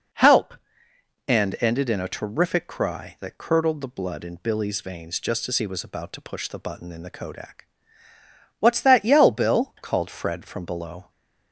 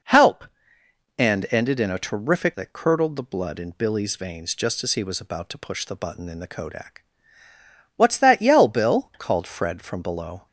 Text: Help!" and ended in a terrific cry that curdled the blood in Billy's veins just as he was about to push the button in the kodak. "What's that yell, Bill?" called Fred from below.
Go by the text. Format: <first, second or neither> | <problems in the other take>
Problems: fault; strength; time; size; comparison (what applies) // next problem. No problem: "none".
first | skips "cry"; at 2.5 s